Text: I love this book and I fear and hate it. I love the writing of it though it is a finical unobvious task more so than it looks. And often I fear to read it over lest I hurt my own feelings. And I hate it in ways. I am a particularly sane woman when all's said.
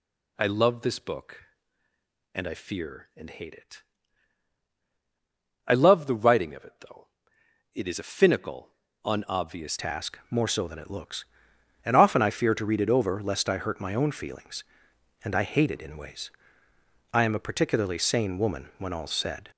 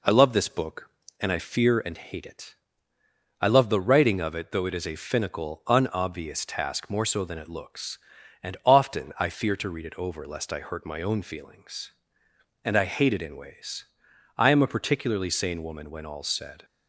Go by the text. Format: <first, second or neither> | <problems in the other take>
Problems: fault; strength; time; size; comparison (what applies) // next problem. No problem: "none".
second | pauses between "though" and "it"; noticeable; at 7.0 s; 0.66 s long // pauses between "finical" and "unobvious"; slight; at 8.7 s; 0.34 s long // changes voice at "task"; from 9.7 s on; 9.8 s long